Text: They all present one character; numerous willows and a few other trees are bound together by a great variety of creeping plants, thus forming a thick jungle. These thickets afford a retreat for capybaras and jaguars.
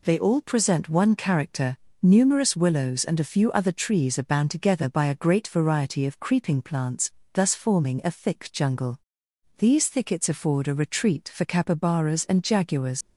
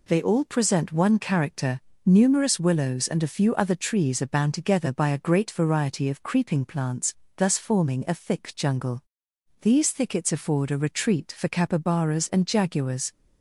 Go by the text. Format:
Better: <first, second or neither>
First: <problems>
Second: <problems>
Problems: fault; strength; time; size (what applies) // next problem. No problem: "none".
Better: second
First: leaves "jaguars" unfinished; at 13.0 s; 70 ms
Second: none